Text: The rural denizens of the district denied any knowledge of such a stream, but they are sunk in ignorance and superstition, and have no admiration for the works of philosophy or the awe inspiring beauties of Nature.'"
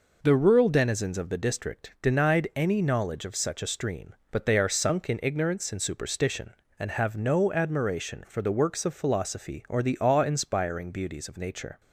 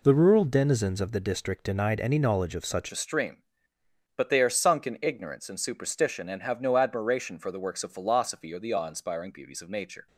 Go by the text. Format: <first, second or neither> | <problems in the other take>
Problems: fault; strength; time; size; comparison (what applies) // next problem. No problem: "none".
first | changes voice at "a"; from 2.9 s on; 7.1 s long